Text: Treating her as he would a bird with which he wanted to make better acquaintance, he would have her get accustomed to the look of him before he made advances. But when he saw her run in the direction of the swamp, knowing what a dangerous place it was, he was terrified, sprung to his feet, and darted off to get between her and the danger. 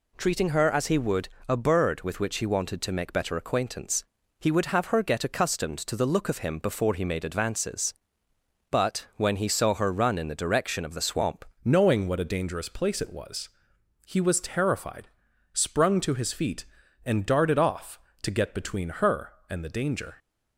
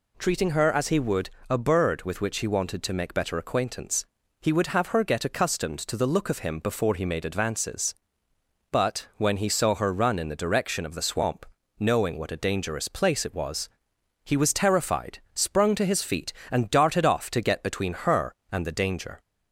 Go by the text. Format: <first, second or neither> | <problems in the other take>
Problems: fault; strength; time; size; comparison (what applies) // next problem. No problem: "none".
second | pauses between "would" and "a"; slight; at 1.2 s; 0.20 s long; slight in the second // changes voice at "knowing"; from 11.6 s on; 8.5 s long